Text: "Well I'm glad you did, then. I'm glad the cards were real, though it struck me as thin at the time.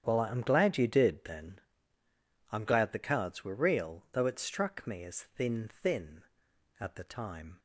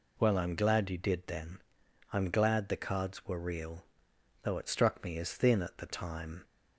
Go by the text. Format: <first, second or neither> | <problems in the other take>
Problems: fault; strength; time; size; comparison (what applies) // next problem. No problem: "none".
second | starts louder than the rest; strong; until 1.0 s; 9 dB // says "thin" twice; at 5.6 s